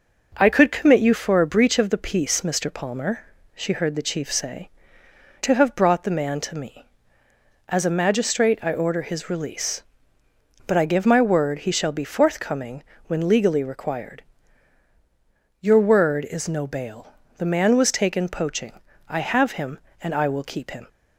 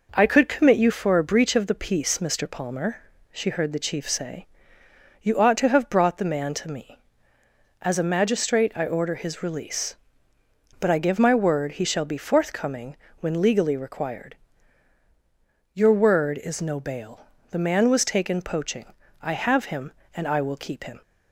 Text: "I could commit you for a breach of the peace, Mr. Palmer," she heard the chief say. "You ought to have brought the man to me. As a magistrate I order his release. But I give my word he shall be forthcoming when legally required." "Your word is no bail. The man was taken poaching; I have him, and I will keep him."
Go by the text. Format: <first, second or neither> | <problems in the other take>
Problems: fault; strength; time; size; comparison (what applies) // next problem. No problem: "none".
second | skips "You ought"; at 5.0 s // pauses between "forthcoming" and "when"; slight; at 12.8 s; 0.22 s long; slight in the second